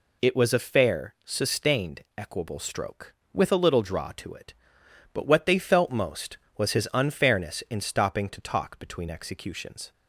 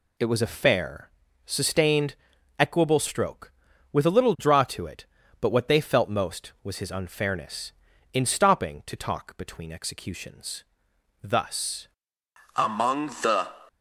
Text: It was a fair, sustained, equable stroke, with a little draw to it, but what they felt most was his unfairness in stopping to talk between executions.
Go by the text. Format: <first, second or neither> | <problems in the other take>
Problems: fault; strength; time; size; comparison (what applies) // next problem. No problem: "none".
first | goes on to say "Thus Among the"; strong; from 11.2 s on; 2.2 s long